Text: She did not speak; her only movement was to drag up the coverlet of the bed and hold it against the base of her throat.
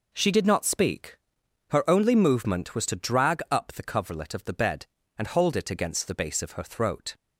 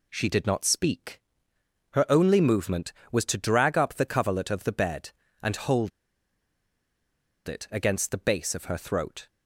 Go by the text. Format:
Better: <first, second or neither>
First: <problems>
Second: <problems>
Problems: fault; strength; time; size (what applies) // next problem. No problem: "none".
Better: first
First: none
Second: pauses between "hold" and "it"; strong; at 5.9 s; 1.5 s long